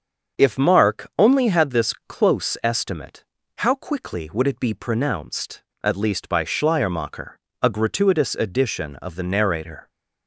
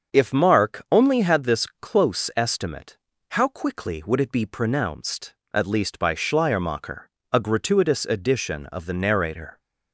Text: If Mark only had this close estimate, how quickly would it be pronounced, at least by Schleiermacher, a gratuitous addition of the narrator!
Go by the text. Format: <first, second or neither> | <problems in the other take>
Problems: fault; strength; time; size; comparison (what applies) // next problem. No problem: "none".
neither | starts louder than the rest; the same in both // pauses between "this" and "close"; slight; the same in both